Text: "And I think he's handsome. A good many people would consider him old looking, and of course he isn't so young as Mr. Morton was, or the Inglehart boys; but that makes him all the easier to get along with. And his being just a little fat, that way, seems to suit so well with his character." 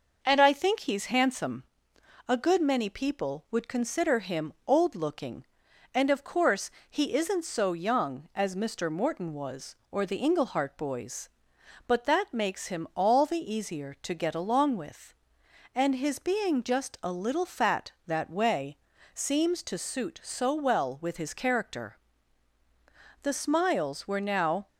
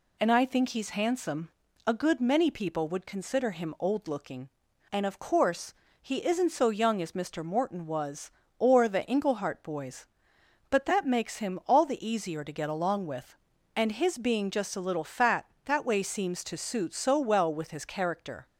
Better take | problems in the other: second | pauses between "course" and "he"; slight; at 6.6 s; 0.18 s long; slight in the second // goes on to say "The smiles were now"; from 23.2 s on; 1.4 s long

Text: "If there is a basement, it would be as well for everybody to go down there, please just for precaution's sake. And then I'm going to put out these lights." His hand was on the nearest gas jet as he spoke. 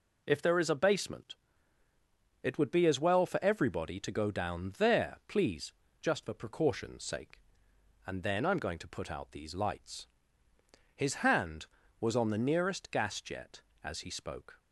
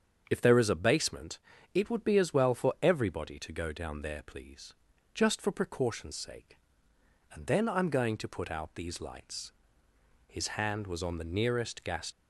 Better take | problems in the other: first | starts louder than the rest; strong; until 1.3 s; 7.5 dB // pauses between "please" and "just"; at 4.7 s; 0.38 s long; slight in the first // stops before "jet as he spoke"; at 12.1 s

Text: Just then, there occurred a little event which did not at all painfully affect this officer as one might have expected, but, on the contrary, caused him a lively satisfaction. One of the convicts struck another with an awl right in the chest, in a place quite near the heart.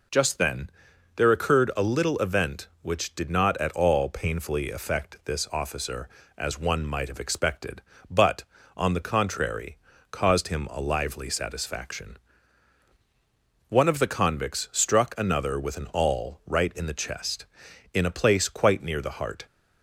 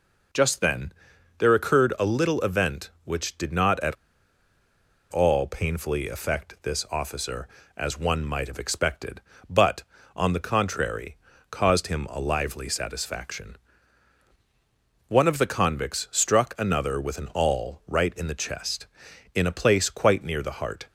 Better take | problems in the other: first | pauses between "at" and "all"; at 3.9 s; 1.1 s long

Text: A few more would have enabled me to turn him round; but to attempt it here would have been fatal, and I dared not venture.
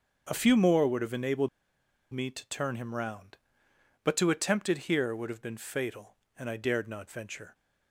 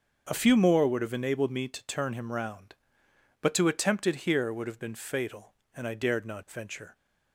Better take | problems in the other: second | starts louder than the rest; until 1.3 s; 6.5 dB; also in the second // pauses between "enabled" and "me"; noticeable; at 1.4 s; 0.65 s long

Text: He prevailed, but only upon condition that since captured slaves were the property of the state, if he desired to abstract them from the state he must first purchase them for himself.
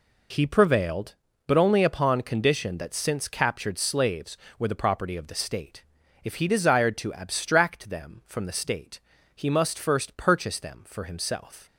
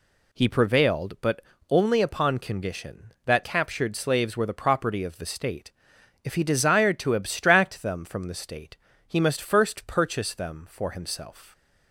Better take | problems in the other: first | pauses between "but" and "only"; slight; at 1.4 s; 0.28 s long // skips "since"; at 3.4 s // pauses between "state" and "he"; slight; at 8.7 s; 0.32 s long; slight in the first

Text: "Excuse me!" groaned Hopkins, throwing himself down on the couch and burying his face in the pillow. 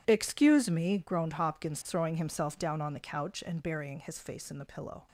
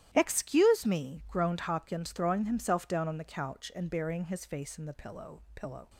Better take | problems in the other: first | starts louder than the rest; strong; until 1.1 s; 12.5 dB // says "pillow" twice; at 5.5 s

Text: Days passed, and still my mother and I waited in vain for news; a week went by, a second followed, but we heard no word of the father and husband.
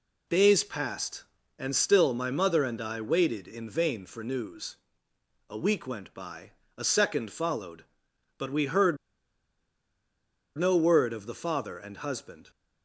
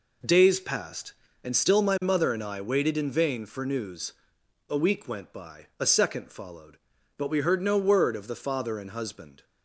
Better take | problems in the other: second | pauses between "heard" and "no"; strong; at 8.9 s; 1.6 s long

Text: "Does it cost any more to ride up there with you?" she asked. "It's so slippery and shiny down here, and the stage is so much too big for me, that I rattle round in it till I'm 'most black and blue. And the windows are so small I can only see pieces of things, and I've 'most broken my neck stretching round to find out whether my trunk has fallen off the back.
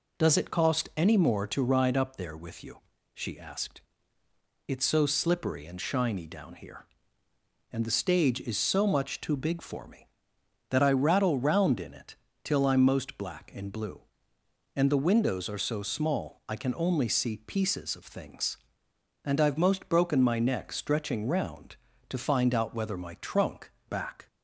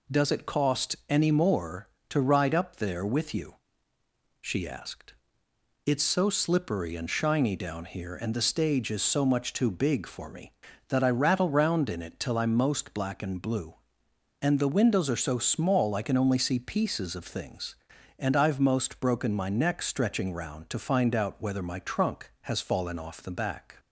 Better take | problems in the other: second | pauses between "it" and "till"; slight; at 12.1 s; 0.28 s long // skips "has fallen off the"; at 23.7 s

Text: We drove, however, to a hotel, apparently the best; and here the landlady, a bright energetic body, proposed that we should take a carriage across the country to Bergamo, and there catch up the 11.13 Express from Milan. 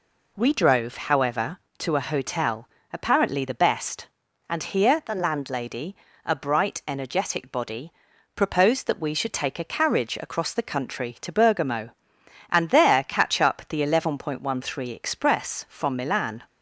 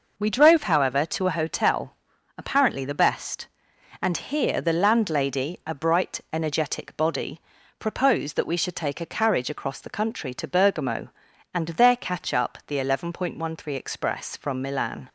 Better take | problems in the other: neither | none

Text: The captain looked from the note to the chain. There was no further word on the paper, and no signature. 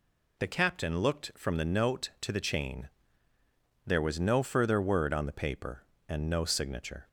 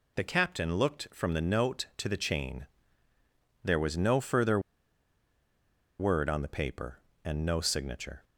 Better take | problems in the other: first | pauses between "further" and "word"; strong; at 4.5 s; 1.3 s long

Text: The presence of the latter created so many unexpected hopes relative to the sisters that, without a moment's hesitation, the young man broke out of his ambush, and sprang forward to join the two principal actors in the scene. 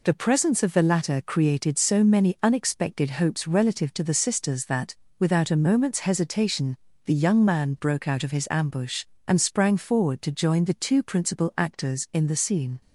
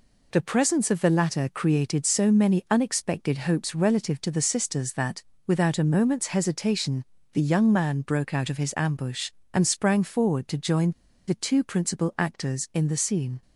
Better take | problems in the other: first | pauses between "join" and "the"; at 10.9 s; 0.37 s long

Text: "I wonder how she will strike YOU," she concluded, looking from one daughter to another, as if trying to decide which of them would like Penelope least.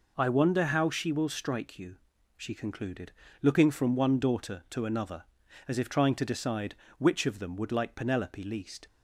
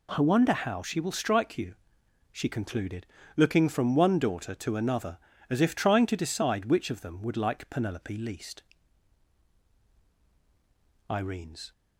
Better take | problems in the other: first | goes on to say "Irene's"; noticeable; from 11.0 s on; 0.64 s long

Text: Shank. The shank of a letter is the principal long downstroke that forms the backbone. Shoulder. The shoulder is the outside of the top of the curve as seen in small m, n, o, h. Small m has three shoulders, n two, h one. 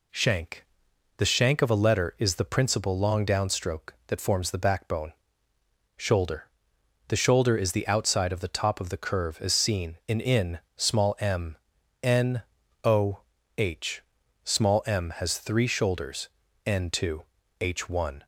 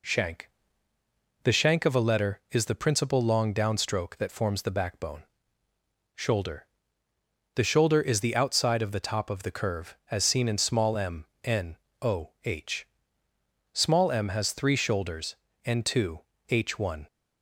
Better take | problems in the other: second | says "in" twice; at 10.2 s

